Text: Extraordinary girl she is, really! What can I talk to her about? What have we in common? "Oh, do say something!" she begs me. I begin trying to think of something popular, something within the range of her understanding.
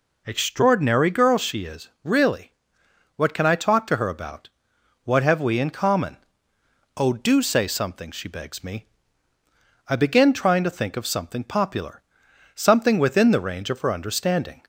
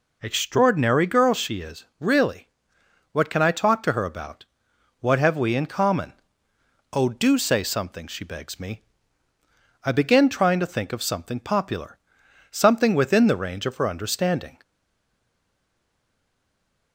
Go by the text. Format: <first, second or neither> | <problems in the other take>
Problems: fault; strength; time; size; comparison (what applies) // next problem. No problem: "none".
first | stays silent after the last word; from 14.6 s on; 2.3 s long